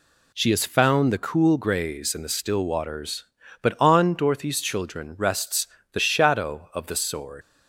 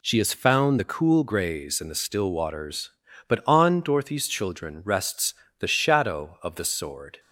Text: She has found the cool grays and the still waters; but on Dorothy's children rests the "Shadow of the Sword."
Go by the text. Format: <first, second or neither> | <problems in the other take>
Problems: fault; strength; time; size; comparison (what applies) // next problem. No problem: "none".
second | pauses between "rests" and "the"; slight; at 5.6 s; 0.26 s long; slight in the second // leaves "Sword" unfinished; at 7.4 s; 95 ms